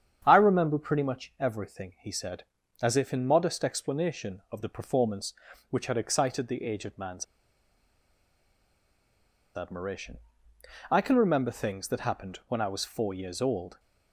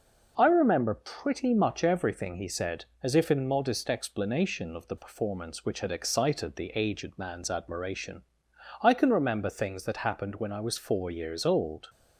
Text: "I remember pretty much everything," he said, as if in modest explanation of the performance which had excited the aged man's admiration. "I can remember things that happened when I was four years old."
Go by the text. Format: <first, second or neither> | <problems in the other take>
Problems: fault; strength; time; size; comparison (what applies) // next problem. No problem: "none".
second | starts louder than the rest; strong; until 1.2 s; 8.5 dB // pauses between "man's" and "admiration"; strong; at 7.2 s; 2.3 s long